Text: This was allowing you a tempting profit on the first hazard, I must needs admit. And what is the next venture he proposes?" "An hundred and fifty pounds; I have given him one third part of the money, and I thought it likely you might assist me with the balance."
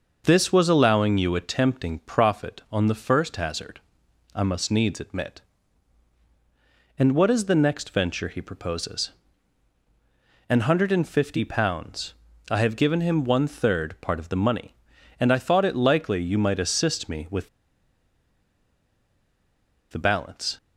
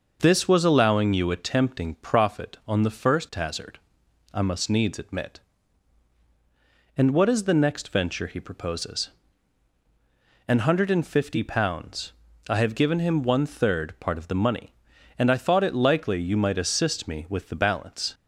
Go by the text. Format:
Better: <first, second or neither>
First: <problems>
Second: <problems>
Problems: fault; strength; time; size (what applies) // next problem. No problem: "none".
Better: second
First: pauses between "with" and "the"; strong; at 17.4 s; 2.4 s long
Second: none